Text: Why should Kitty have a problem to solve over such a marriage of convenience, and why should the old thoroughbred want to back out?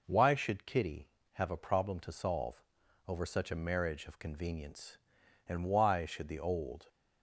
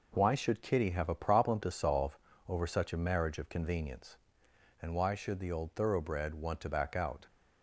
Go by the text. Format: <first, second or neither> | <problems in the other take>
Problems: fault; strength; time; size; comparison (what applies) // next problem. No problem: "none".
second | pauses between "solve" and "over"; noticeable; at 2.6 s; 0.46 s long; slight in the second // stops before "thoroughbred want to back out"; at 6.8 s